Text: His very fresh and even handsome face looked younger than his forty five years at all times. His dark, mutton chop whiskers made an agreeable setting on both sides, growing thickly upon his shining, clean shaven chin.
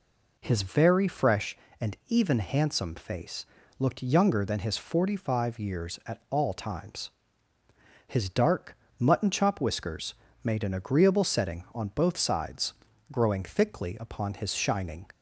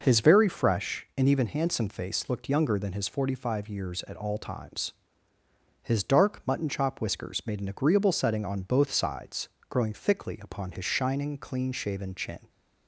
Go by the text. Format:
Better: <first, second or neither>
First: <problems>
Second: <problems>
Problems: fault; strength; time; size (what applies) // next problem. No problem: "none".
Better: second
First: pauses between "face" and "looked"; slight; at 3.4 s; 0.34 s long // pauses between "whiskers" and "made"; slight; at 10.1 s; 0.30 s long // stops before "clean shaven chin"; at 15.1 s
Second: none